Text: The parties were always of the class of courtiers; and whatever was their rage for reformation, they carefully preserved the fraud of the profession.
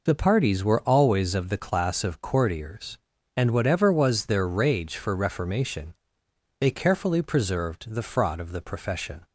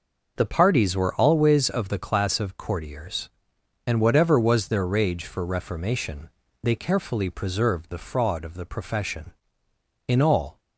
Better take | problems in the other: first | goes on to say "In all"; from 10.0 s on; 0.52 s long

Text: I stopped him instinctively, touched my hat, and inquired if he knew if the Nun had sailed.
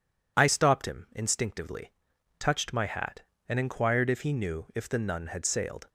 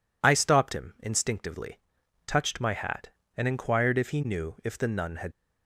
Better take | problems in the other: first | stops before "sailed"; at 5.3 s

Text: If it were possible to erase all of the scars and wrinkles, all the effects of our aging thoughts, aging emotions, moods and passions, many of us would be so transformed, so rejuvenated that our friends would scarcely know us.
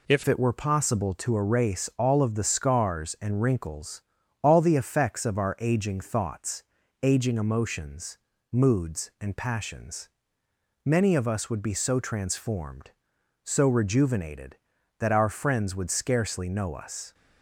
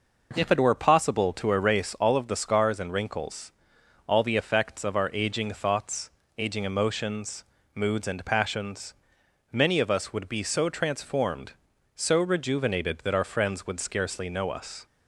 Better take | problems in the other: second | changes voice at "it"; from 0.2 s on; 16.9 s long

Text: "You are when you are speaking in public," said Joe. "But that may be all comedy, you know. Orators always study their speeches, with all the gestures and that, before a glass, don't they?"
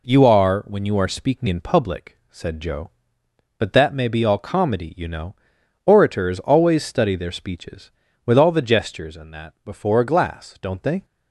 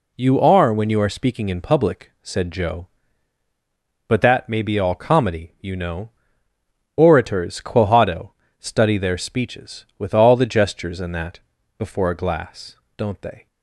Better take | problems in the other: first | says "quohado" for "always"; at 7.5 s

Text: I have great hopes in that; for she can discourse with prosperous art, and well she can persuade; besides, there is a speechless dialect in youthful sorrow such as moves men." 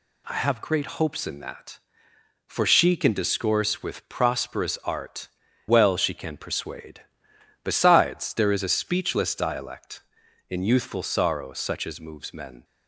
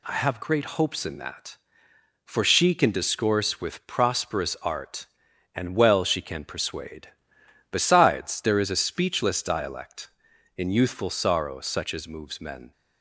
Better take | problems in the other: second | skips "and"; at 5.4 s

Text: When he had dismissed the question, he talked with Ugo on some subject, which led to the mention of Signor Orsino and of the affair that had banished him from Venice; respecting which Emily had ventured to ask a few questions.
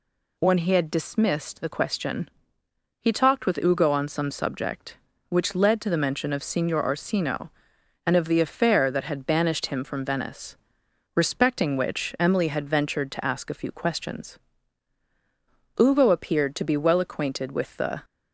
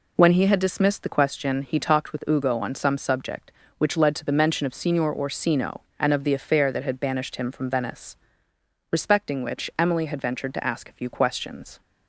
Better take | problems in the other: second | goes on to say "Ugo appeared to be well acquainted with the"; strong; from 15.7 s on; 2.2 s long

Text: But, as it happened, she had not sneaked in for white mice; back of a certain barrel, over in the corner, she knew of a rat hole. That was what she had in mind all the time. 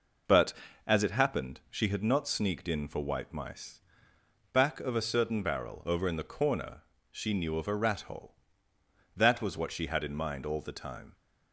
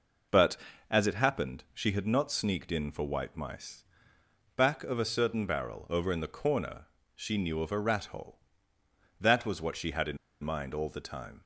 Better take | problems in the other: first | pauses between "in" and "mind"; slight; at 10.1 s; 0.25 s long

